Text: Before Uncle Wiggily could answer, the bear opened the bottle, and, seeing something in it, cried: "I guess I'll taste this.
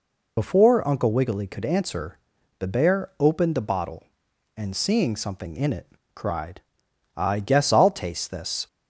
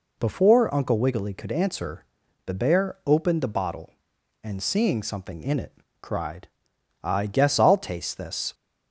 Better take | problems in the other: second | loses the start of "Before"; at 0.3 s; 55 ms

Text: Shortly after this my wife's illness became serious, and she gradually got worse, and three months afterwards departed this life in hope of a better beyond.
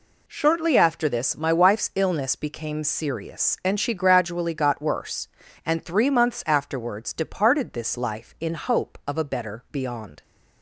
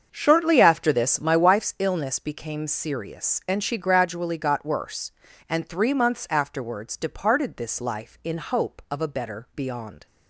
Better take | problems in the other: first | starts louder than the rest; until 1.6 s; 7 dB

